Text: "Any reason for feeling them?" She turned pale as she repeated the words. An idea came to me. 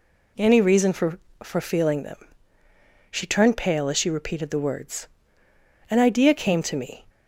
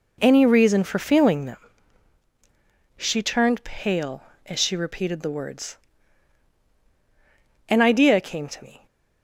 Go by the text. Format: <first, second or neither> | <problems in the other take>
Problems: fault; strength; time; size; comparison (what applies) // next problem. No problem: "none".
second | says "for" twice; at 1.4 s